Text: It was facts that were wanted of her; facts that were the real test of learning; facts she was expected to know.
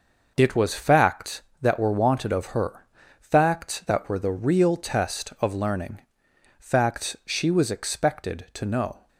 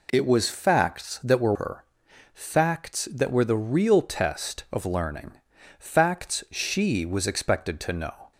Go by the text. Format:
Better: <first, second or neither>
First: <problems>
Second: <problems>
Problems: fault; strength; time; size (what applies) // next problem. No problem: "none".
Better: first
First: none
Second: skips "wanted of"; at 1.5 s